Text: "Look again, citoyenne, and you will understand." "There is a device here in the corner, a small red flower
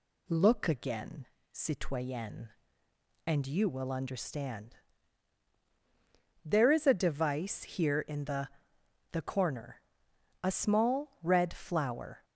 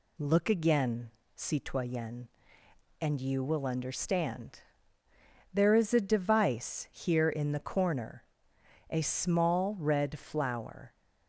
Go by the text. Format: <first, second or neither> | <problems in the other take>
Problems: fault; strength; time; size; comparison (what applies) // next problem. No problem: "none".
second | says "the" twice; at 9.1 s